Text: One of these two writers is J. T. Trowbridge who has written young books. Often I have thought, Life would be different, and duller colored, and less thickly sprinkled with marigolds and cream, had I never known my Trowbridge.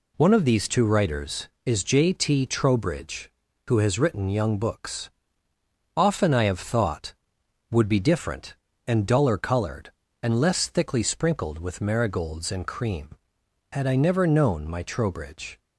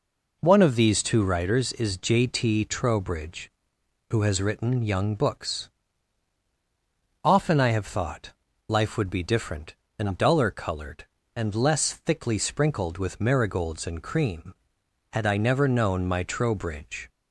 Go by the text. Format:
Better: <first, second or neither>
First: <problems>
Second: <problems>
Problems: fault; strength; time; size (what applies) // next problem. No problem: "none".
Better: second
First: skips "Life"; at 7.4 s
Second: none